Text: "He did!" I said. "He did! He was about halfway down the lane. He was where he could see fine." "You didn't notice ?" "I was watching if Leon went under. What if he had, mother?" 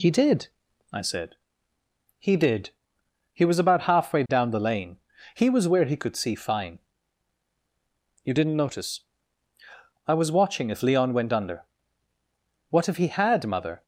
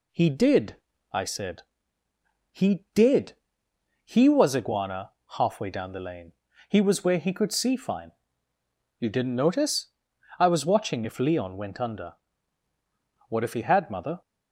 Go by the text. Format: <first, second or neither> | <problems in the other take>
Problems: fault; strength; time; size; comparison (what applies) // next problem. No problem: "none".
first | says "iguana" for "about"; at 4.5 s